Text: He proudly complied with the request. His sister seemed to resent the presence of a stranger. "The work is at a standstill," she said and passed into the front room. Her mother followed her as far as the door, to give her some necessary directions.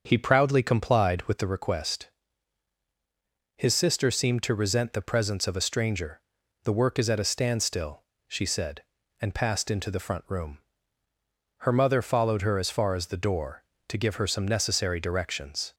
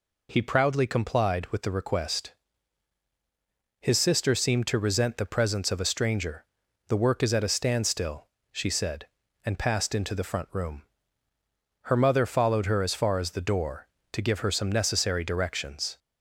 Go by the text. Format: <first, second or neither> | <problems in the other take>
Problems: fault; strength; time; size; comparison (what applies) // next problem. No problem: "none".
second | starts louder than the rest; until 1.6 s; 6.5 dB